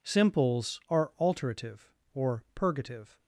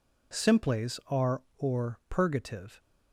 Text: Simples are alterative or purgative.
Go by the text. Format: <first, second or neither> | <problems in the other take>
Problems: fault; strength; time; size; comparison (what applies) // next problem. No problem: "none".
first | skips "alterative"; at 1.5 s